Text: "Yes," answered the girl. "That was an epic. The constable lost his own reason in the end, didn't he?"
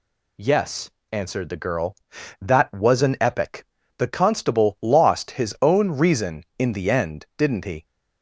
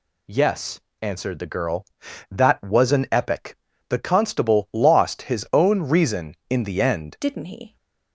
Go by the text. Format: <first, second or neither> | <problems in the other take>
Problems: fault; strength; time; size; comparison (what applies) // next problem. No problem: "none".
first | changes voice at "didn't"; from 7.2 s on; 0.5 s long